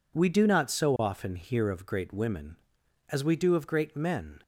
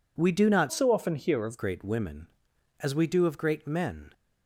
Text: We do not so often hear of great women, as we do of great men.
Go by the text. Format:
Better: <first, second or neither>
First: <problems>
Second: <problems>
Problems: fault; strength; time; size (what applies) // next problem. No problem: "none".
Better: first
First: none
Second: changes voice from "so" to "of"; from 0.7 to 1.5 s; 0.8 s long